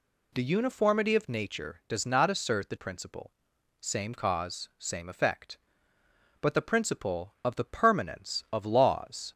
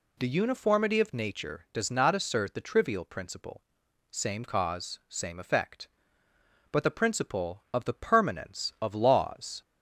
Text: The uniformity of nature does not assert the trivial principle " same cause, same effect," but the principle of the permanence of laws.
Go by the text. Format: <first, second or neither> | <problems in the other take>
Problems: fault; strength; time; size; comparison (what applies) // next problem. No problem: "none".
second | skips "trivial"; at 2.7 s